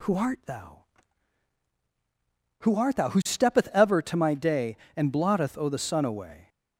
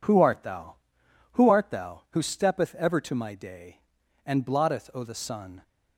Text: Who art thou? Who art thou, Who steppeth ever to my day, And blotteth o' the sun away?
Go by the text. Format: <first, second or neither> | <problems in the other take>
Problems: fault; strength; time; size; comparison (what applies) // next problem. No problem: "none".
first | stops before "away"; at 5.6 s